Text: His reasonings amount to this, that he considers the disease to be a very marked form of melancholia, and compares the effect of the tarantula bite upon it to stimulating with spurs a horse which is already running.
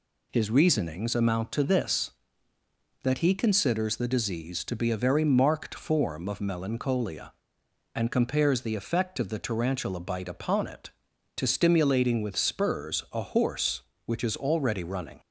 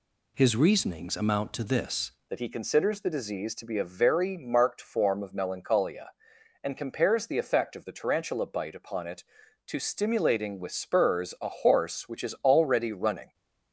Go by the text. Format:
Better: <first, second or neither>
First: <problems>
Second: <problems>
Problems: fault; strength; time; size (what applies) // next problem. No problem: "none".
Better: first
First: none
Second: changes voice at "that"; from 2.2 s on; 11.1 s long